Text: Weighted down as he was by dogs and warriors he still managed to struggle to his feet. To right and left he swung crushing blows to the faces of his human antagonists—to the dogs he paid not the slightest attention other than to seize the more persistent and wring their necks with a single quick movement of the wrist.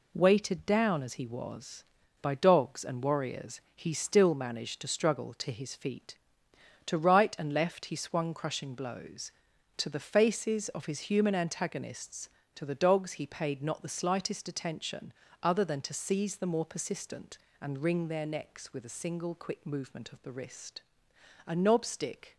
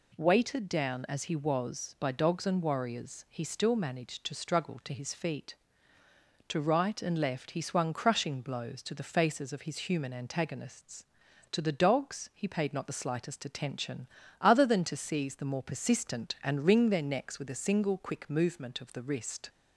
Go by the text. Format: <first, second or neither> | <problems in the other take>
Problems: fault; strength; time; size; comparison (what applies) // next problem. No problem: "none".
second | pauses between "attention" and "other"; slight; at 15.1 s; 0.30 s long; slight in the second // goes on to say "A knob stick"; noticeable; from 21.4 s on; 0.92 s long